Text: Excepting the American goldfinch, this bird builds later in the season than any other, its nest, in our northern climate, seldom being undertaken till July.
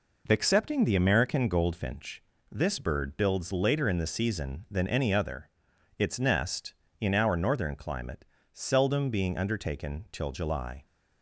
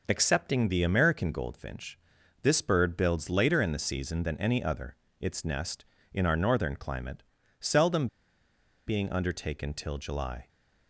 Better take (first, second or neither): first